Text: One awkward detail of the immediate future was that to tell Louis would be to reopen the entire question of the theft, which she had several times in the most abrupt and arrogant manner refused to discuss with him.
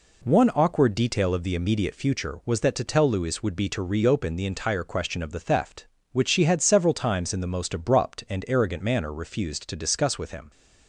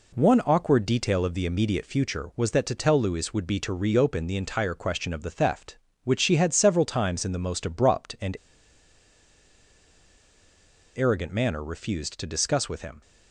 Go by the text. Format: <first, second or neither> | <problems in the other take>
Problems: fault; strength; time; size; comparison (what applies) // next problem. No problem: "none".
first | pauses between "and" and "arrogant"; strong; at 8.3 s; 2.5 s long